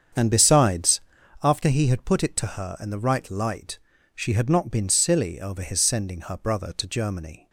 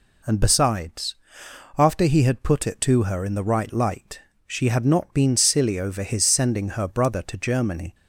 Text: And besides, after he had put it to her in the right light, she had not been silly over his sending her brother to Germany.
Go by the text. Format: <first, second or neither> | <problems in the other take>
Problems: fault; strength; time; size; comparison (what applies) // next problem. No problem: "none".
second | starts louder than the rest; strong; until 1.5 s; 7.5 dB